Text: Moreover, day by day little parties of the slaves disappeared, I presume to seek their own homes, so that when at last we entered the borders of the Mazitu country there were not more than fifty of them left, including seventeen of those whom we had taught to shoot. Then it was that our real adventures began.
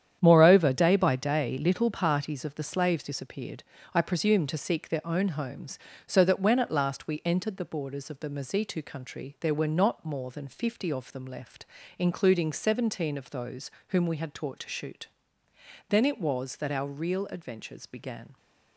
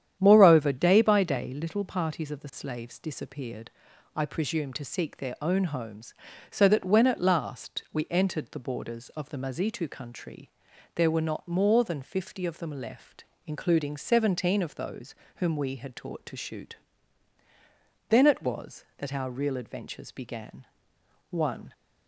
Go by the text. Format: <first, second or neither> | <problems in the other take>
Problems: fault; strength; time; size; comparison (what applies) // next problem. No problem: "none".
first | starts louder than the rest; strong; until 1.2 s; 9.5 dB; strong in the first // pauses between "country" and "there"; noticeable; at 10.5 s; 0.46 s long // pauses between "those" and "whom"; slight; at 15.1 s; 0.22 s long; slight in the first // goes on to say "One"; slight; from 21.3 s on; 0.42 s long